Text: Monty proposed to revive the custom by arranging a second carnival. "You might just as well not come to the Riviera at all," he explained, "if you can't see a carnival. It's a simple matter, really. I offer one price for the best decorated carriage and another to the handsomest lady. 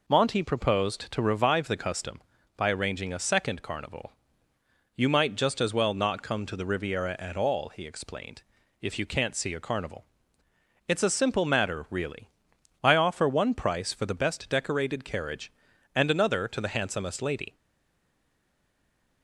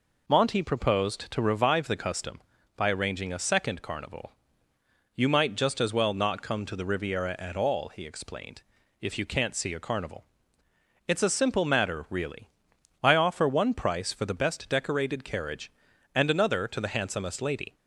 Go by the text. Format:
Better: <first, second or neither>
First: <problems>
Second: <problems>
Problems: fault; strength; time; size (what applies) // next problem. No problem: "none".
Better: second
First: stays silent after the last word; noticeable; from 17.5 s on; 1.7 s long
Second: none